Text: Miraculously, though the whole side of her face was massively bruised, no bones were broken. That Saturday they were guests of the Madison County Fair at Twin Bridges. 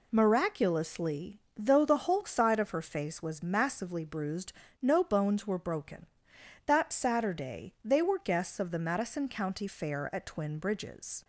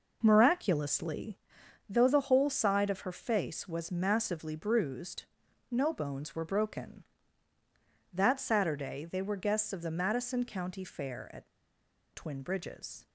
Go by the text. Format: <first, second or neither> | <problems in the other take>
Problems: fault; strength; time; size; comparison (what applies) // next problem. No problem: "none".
first | pauses between "at" and "Twin"; noticeable; at 11.4 s; 0.66 s long